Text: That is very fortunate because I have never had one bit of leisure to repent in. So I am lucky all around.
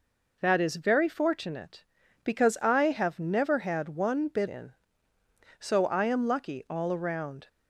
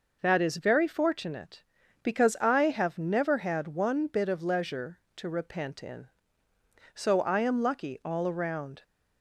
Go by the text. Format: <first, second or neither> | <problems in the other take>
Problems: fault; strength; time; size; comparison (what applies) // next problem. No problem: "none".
second | skips "of leisure to repent"; at 4.4 s